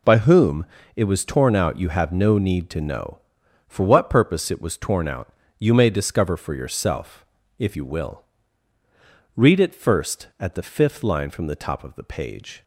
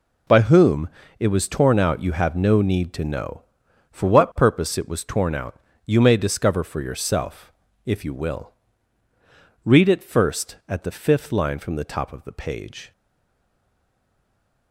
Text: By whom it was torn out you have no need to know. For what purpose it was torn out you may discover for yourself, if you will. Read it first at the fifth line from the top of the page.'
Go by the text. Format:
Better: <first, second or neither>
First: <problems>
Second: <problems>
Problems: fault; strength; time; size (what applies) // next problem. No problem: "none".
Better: first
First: pauses between "whom" and "it"; slight; at 0.6 s; 0.28 s long // pauses between "out" and "you"; slight; at 5.3 s; 0.26 s long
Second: pauses between "whom" and "it"; slight; at 0.9 s; 0.28 s long // pauses between "out" and "you"; slight; at 5.5 s; 0.26 s long // stays silent after the last word; noticeable; from 12.9 s on; 1.8 s long